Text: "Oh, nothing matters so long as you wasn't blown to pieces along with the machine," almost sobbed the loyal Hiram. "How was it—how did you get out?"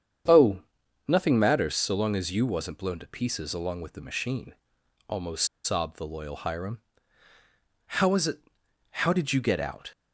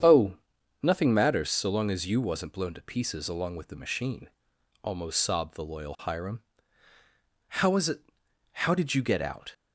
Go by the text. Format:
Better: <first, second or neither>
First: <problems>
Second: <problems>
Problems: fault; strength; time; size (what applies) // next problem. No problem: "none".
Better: second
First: starts louder than the rest; strong; until 1.7 s; 8 dB // pauses between "almost" and "sobbed"; slight; at 5.4 s; 0.18 s long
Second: starts louder than the rest; strong; until 1.5 s; 8 dB